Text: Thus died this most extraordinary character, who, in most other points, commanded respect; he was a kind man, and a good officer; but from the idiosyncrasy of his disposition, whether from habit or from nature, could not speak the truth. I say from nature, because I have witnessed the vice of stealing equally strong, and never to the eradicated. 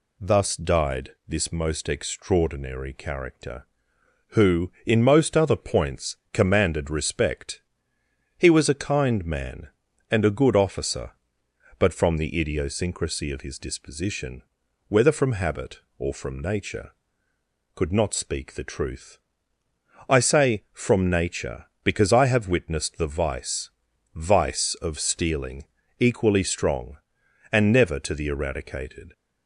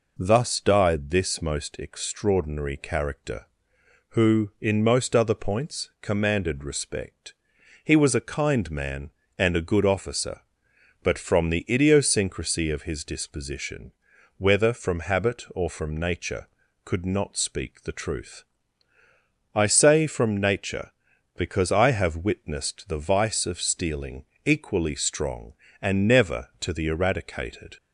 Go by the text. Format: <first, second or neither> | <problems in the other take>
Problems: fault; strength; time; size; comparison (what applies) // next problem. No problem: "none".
second | pauses between "died" and "this"; slight; at 1.1 s; 0.18 s long // says "vice" twice; at 24.1 s // pauses between "stealing" and "equally"; slight; at 25.6 s; 0.32 s long; slight in the second